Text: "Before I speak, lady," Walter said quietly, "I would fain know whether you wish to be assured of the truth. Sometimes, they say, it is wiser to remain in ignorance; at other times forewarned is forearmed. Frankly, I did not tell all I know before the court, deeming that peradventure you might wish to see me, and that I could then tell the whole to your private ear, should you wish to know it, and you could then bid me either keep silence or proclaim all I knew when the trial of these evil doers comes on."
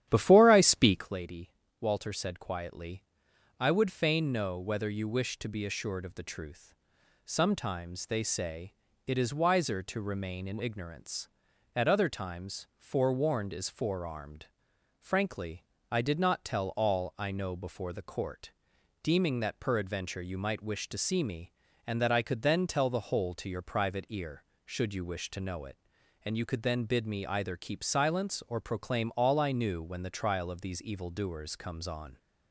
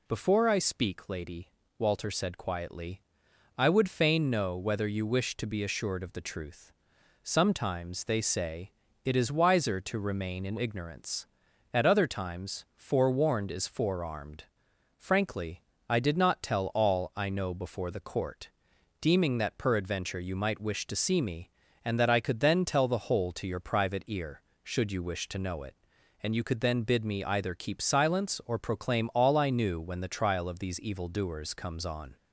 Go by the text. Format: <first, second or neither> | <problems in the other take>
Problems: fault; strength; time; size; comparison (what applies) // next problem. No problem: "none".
second | starts louder than the rest; strong; until 1.2 s; 11 dB